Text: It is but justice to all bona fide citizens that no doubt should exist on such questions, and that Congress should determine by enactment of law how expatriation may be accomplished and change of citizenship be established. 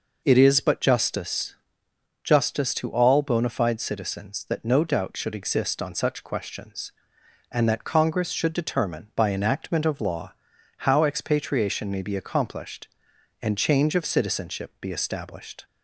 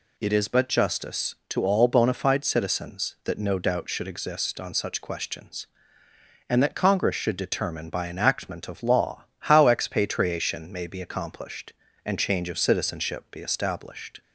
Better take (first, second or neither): second